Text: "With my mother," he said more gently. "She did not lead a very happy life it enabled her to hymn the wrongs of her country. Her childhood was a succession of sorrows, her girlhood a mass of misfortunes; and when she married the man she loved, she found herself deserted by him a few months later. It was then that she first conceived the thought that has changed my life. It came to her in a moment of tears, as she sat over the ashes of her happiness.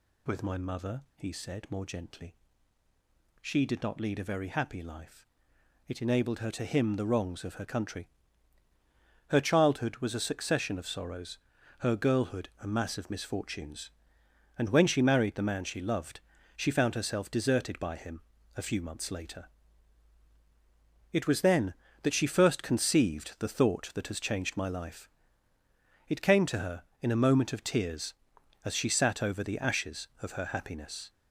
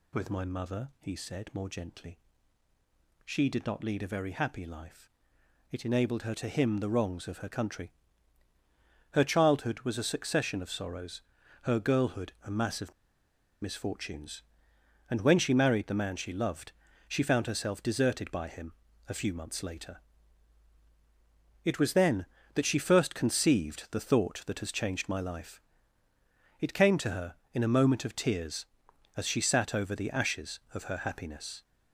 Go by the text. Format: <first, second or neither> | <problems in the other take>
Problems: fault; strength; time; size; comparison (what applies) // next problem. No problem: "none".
first | pauses between "life" and "it"; noticeable; at 5.0 s; 0.62 s long; noticeable in the first // pauses between "of" and "misfortunes"; noticeable; at 12.9 s; 0.69 s long // pauses between "him" and "a"; slight; at 18.7 s; 0.34 s long; slight in the first